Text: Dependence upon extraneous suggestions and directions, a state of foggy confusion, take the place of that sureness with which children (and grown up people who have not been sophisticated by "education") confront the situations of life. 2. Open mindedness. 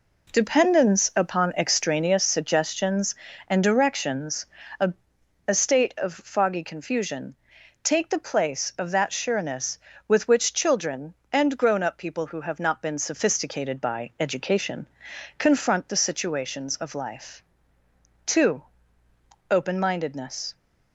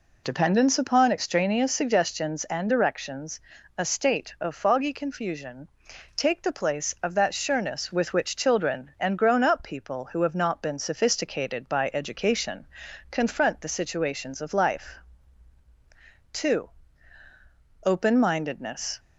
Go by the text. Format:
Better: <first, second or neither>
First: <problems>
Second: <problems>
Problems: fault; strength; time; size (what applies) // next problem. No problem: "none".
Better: second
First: says "a" twice; at 5.4 s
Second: none